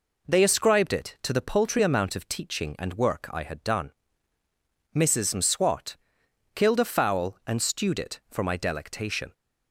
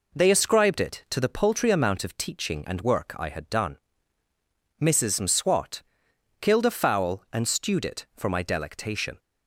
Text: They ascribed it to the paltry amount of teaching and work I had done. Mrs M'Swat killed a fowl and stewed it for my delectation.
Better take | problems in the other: neither | pauses between "M'Swat" and "killed"; noticeable; the same in both

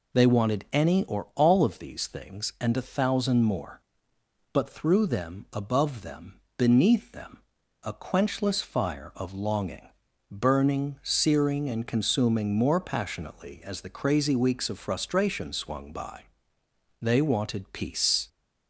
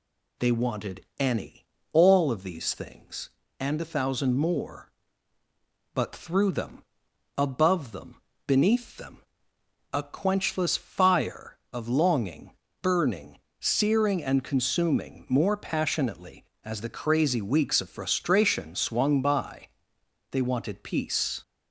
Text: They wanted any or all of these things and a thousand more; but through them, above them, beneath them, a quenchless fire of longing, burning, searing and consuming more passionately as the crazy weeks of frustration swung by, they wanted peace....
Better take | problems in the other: first | skips "or"; at 1.7 s

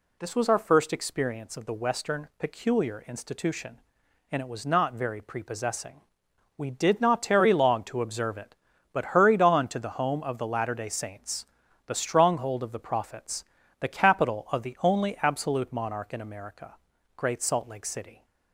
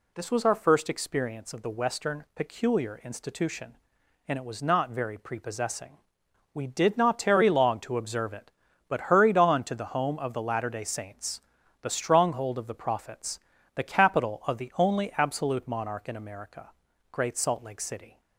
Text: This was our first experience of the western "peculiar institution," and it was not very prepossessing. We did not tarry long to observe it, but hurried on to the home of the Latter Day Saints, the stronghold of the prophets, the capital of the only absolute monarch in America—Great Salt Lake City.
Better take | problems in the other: neither | none

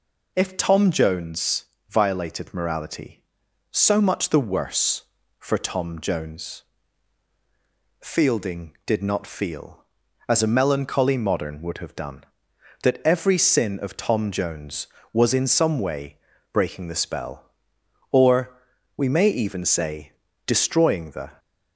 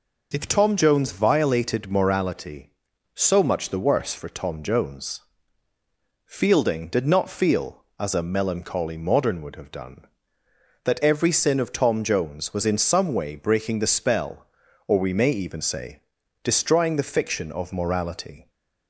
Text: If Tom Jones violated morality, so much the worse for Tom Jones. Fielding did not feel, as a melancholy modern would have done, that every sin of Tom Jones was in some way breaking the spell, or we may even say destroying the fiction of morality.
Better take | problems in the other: second | pauses between "Jones" and "violated"; slight; at 1.6 s; 0.24 s long // pauses between "way" and "breaking"; slight; at 16.1 s; 0.36 s long // pauses between "or" and "we"; at 18.5 s; 0.42 s long // pauses between "say" and "destroying"; slight; at 20.1 s; 0.34 s long; also in the second // stops before "fiction of morality"; at 21.3 s

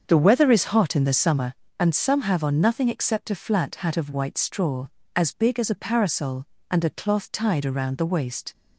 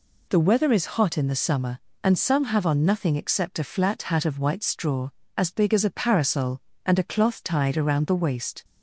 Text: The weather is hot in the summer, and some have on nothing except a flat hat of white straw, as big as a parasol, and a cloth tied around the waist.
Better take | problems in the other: second | starts louder than the rest; until 1.5 s; 7 dB

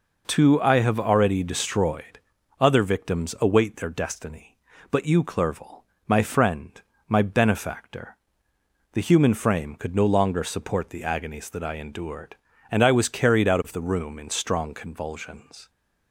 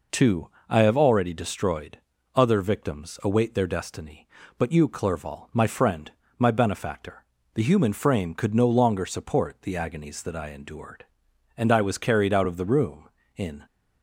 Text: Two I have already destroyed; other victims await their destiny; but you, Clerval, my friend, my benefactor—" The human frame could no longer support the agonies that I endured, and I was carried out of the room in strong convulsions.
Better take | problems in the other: first | pauses between "Two" and "I"; slight; at 0.4 s; 0.18 s long // stops before "strong convulsions"; at 13.6 s

